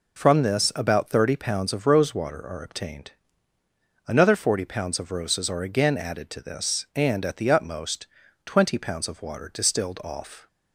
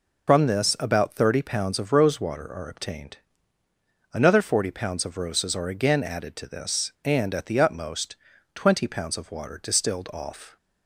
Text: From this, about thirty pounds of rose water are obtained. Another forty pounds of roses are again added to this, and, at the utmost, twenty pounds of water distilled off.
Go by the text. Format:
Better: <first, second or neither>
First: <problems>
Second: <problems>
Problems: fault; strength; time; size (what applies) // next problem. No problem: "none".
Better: first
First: none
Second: loses the start of "From"; at 0.2 s; 75 ms